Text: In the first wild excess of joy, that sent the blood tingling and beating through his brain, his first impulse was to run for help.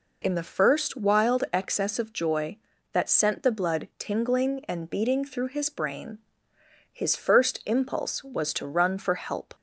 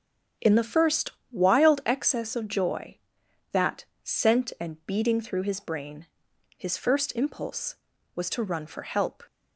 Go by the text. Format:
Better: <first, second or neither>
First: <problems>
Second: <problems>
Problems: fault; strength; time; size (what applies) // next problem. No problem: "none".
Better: first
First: none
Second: starts louder than the rest; strong; until 1.6 s; 7.5 dB // pauses between "first" and "wild"; slight; at 1.0 s; 0.22 s long // pauses between "that" and "sent"; slight; at 3.8 s; 0.18 s long // skips "the blood tingling"; at 4.5 s